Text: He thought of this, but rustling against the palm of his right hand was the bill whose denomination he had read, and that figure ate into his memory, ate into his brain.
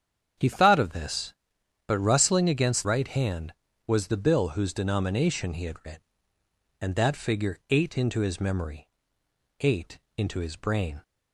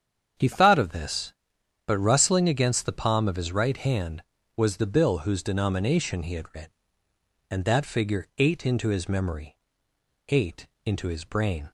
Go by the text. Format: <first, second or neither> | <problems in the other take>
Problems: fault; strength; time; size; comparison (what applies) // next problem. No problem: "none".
second | starts louder than the rest; strong; until 1.9 s; 8 dB; strong in the second // skips "the palm of his"; at 2.8 s // pauses between "ate" and "into"; slight; at 9.9 s; 0.18 s long; slight in the second